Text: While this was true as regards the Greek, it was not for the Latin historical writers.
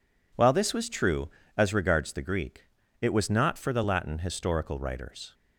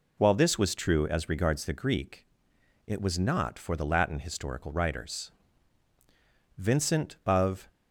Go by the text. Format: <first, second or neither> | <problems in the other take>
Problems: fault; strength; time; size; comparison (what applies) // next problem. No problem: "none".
first | goes on to say "Vincent of"; noticeable; from 6.5 s on; 1.1 s long